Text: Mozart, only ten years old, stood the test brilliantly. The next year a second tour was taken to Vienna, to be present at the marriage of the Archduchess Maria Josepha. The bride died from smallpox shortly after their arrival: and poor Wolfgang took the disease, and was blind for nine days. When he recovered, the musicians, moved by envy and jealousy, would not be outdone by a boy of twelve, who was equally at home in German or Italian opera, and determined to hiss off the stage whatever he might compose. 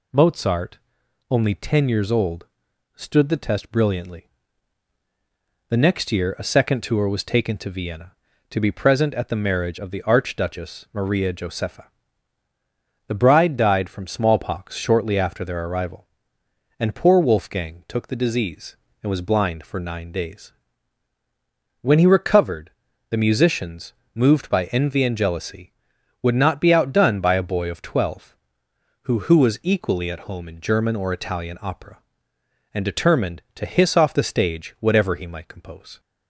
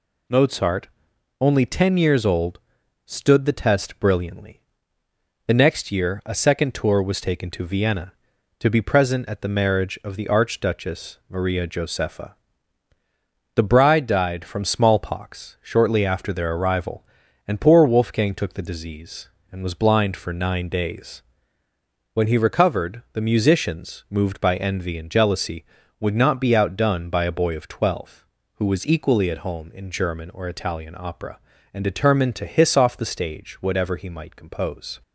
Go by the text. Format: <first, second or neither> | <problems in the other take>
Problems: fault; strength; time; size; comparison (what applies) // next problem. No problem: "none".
second | says "who" twice; at 29.2 s